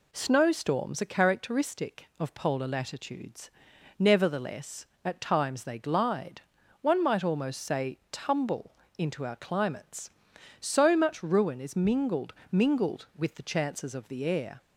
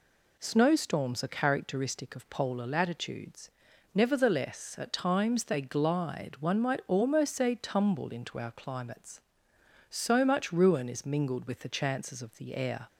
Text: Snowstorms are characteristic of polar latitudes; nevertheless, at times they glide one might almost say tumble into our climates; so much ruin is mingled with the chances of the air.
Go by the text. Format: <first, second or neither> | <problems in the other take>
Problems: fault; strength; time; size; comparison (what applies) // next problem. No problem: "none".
second | pauses between "glide" and "one"; at 6.4 s; 0.40 s long // pauses between "tumble" and "into"; slight; at 8.7 s; 0.24 s long // says "mingled" twice; at 12.5 s